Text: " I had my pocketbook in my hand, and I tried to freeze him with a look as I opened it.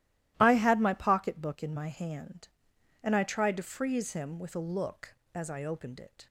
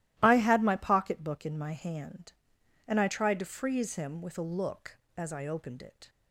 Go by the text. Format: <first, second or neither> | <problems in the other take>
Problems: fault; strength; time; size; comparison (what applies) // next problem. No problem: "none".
neither | starts louder than the rest; strong; the same in both